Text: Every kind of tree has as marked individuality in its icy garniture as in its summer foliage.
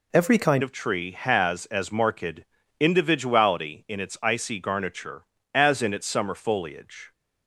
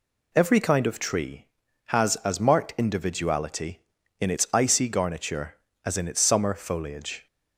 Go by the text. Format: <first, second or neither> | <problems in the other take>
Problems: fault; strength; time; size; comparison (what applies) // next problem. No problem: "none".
second | changes voice at "of"; from 0.6 s on; 6.5 s long // pauses between "marked" and "individuality"; at 2.4 s; 0.38 s long